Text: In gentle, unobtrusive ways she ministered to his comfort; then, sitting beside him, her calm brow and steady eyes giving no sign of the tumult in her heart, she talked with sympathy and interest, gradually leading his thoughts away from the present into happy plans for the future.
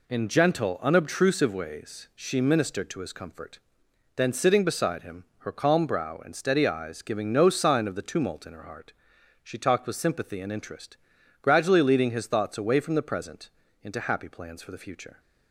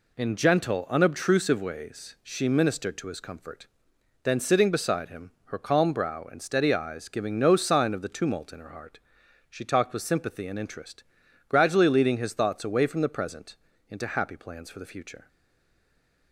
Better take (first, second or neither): first